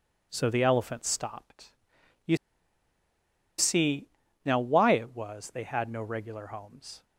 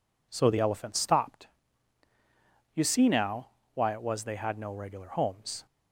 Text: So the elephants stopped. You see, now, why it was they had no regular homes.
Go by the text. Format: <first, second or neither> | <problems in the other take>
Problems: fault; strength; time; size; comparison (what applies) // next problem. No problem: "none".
second | pauses between "You" and "see"; at 2.3 s; 1.2 s long